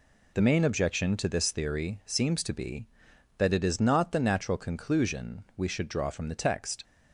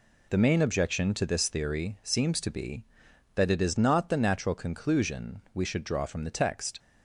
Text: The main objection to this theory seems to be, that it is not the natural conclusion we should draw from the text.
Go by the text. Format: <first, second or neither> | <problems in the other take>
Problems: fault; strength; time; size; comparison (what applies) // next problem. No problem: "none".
neither | none